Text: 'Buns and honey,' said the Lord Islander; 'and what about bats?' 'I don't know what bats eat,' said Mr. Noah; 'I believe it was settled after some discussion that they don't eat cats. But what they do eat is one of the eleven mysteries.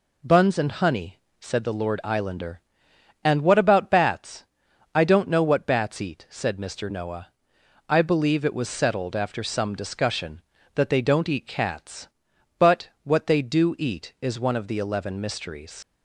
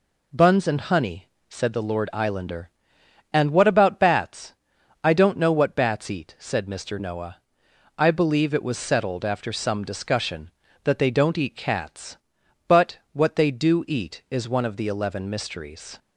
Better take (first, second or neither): second